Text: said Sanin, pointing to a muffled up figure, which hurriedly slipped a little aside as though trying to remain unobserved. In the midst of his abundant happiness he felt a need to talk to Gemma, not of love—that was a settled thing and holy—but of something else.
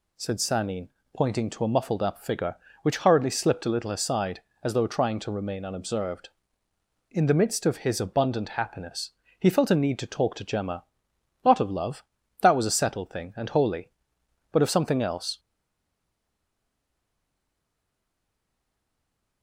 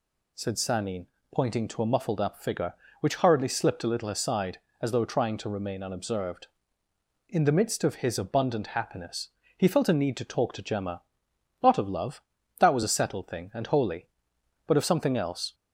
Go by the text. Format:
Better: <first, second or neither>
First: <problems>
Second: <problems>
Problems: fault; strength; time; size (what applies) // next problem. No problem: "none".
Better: second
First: pauses between "happiness" and "he"; slight; at 9.1 s; 0.28 s long // stays silent after the last word; strong; from 15.3 s on; 4.1 s long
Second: pauses between "happiness" and "he"; slight; at 9.2 s; 0.28 s long